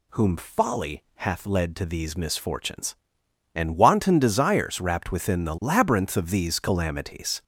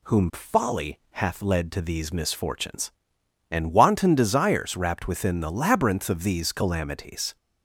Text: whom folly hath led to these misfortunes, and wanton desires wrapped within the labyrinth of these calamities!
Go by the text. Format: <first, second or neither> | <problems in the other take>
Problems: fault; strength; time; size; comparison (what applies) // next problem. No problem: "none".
second | gets louder; noticeable; throughout; 4.5 dB